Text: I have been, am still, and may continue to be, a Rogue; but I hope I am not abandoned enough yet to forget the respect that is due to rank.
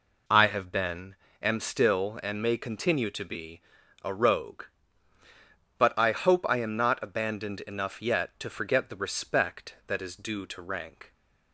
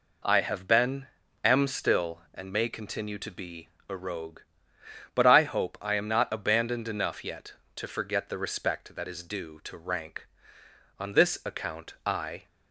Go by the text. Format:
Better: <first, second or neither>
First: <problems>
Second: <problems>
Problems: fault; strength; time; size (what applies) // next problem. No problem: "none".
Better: first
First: none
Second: goes on to say "On this account I"; from 10.9 s on; 1.4 s long